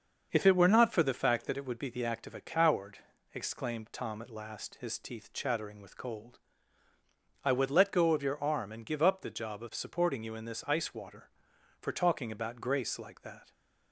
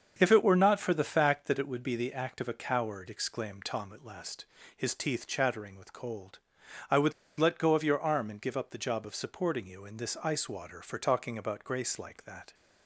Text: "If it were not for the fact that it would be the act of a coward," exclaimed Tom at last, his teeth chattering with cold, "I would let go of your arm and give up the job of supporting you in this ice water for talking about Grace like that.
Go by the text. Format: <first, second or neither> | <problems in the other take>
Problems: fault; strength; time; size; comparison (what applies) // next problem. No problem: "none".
first | starts louder than the rest; until 1.1 s; 7 dB; also in the first // pauses between "would" and "let"; slight; at 7.1 s; 0.24 s long